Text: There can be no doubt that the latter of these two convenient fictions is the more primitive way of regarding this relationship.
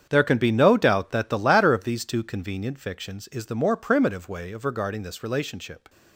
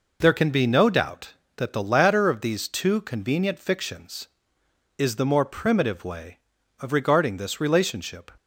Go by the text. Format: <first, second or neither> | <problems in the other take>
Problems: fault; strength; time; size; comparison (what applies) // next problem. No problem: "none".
second | gets quieter; strong; throughout; 13 dB